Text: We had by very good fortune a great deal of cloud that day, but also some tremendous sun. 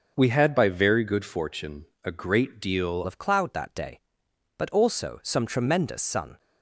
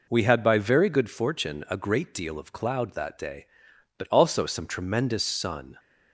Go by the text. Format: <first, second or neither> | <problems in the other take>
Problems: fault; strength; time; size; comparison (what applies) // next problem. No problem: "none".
second | starts louder than the rest; until 1.1 s; 6.5 dB // pauses between "fortune" and "a"; slight; at 1.8 s; 0.18 s long // changes voice at "of"; from 3.0 s on; 3.3 s long